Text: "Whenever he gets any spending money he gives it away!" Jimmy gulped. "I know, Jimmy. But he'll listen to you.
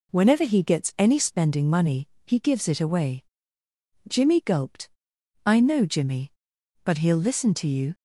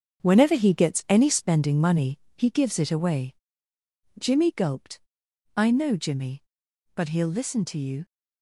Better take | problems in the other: first | gets quieter; strong; throughout; 8 dB // pauses between "money" and "he"; slight; at 2.1 s; 0.18 s long; slight in the first

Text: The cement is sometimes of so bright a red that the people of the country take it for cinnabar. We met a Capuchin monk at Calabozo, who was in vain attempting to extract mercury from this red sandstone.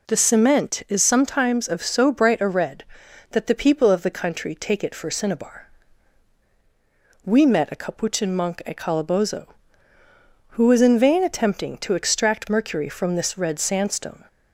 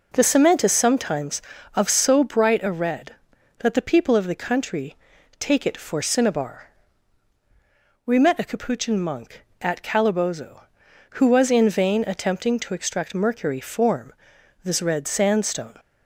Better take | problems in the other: first | pauses between "country" and "take"; at 4.9 s; 0.44 s long // says "form" for "from"; at 13.6 s

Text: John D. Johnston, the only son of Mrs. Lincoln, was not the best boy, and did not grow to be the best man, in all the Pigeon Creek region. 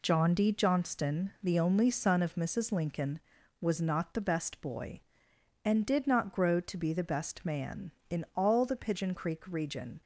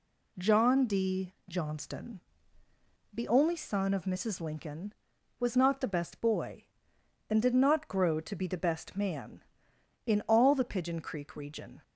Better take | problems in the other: neither | none

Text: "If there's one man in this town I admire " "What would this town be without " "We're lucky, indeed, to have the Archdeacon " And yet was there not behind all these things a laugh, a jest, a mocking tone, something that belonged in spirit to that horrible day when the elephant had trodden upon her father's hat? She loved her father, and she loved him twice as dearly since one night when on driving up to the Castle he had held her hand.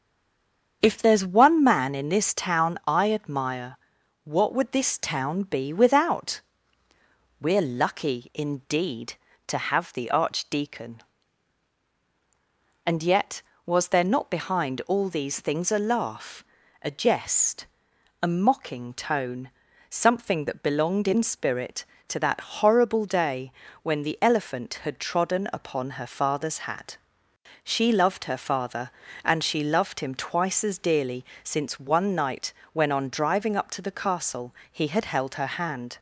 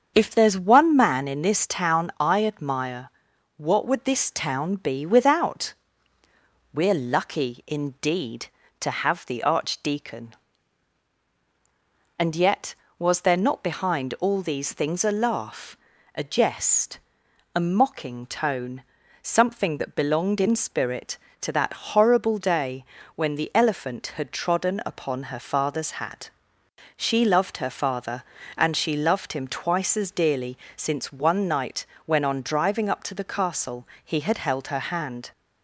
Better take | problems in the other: second | stays silent before the first word; slight; until 0.8 s; 0.8 s long // starts louder than the rest; strong; until 1.8 s; 7.5 dB; strong in the second // pauses between "day" and "when"; slight; at 23.5 s; 0.30 s long; slight in the second // pauses between "dearly" and "since"; slight; at 31.2 s; 0.20 s long; slight in the second // pauses between "night" and "when"; slight; at 32.5 s; 0.20 s long; slight in the second // pauses between "Castle" and "he"; slight; at 34.5 s; 0.16 s long; slight in the second

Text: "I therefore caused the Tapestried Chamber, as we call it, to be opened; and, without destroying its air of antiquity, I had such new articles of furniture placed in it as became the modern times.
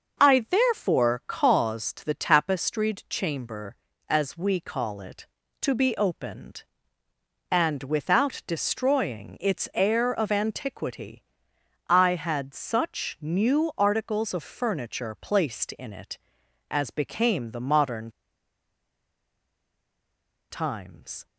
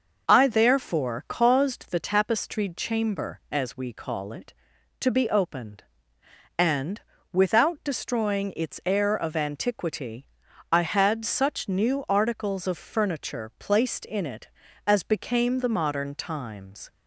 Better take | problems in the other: second | starts louder than the rest; noticeable; until 1.3 s; 6 dB; noticeable in the second // pauses between "modern" and "times"; strong; at 18.0 s; 2.4 s long

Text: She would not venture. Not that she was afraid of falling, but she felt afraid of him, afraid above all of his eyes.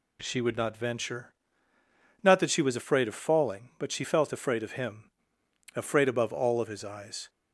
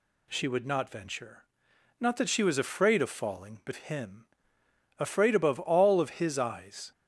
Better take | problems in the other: first | skips "she felt afraid of"; at 3.7 s

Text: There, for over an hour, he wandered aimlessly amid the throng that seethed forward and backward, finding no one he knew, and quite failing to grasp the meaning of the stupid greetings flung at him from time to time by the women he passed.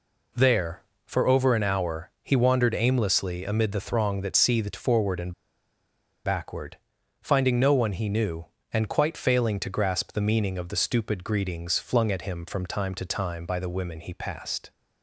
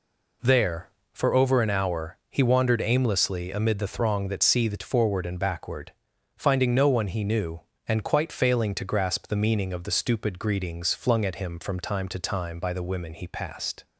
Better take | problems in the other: second | pauses between "and" and "backward"; noticeable; at 5.3 s; 0.92 s long

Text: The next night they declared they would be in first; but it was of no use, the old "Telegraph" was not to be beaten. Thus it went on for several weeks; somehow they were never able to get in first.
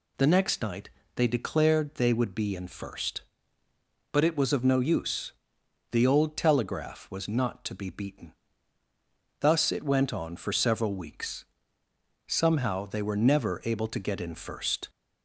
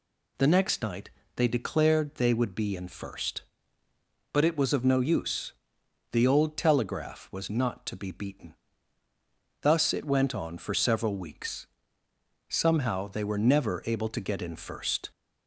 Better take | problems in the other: neither | pauses between "night" and "they"; slight; the same in both

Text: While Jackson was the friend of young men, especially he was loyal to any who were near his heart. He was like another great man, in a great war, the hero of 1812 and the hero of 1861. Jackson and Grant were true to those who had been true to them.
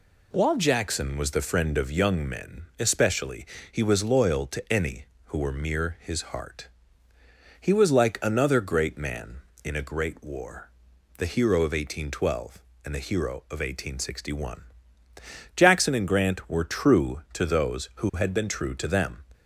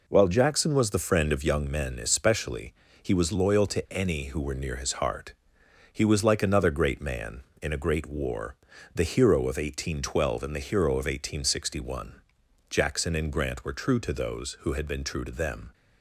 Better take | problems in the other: second | pauses between "especially" and "he"; slight; at 3.4 s; 0.24 s long; slight in the second // says "mere" for "near"; at 5.5 s

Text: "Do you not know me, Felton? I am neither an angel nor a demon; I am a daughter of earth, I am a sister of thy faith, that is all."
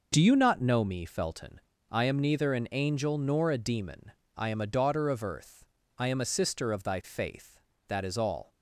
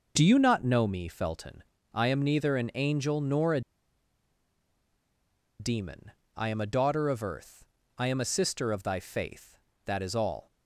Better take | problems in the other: first | pauses between "a" and "demon"; strong; at 3.6 s; 1.9 s long

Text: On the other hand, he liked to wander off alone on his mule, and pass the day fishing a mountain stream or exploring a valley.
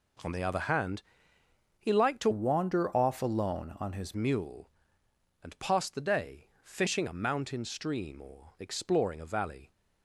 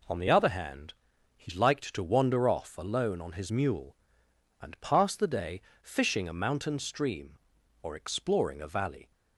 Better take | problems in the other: second | changes voice from "wander" to "his"; from 2.3 to 4.1 s; 1.8 s long // pauses between "day" and "fishing"; slight; at 6.4 s; 0.16 s long; slight in the second

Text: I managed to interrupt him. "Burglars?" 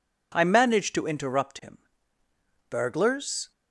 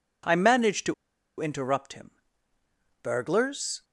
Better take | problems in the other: first | pauses between "to" and "interrupt"; at 0.9 s; 0.45 s long

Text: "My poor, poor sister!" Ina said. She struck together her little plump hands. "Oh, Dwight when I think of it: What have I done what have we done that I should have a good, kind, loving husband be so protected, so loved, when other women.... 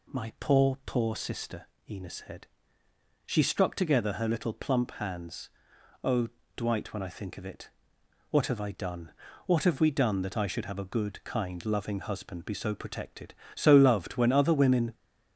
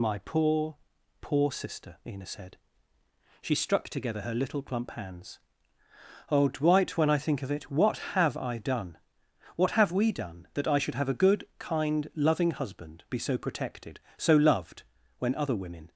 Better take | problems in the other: first | loses the start of "My"; at 0.0 s; 45 ms // pauses between "done" and "what"; noticeable; at 8.9 s; 0.58 s long; slight in the first

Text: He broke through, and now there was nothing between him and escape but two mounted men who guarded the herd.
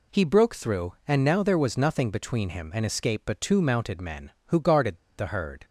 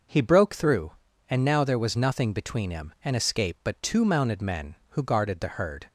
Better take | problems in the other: second | pauses between "guarded" and "the"; slight; at 4.9 s; 0.21 s long

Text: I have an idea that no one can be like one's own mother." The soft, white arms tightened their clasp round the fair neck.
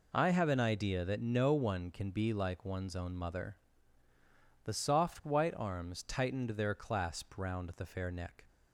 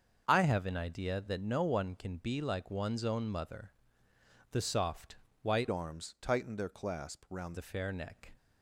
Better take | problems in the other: first | starts louder than the rest; until 1.2 s; 6.5 dB // changes voice from "arms" to "round"; from 5.6 to 7.5 s; 1.9 s long

